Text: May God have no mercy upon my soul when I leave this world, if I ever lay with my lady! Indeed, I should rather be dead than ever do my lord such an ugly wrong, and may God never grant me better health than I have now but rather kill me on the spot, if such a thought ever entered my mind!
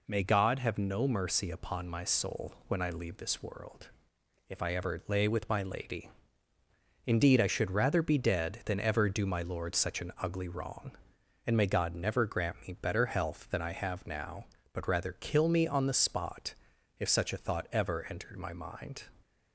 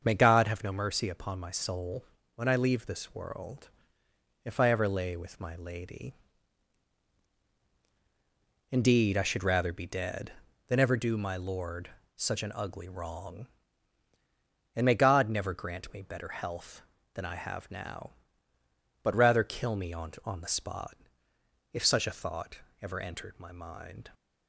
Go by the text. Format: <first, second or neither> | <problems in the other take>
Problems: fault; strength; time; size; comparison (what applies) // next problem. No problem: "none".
first | starts louder than the rest; until 1.0 s; 6.5 dB // pauses between "soul" and "when"; slight; at 2.0 s; 0.32 s long // pauses between "lord" and "such"; slight; at 11.8 s; 0.26 s long // says "on" twice; at 20.2 s // pauses between "thought" and "ever"; slight; at 22.5 s; 0.24 s long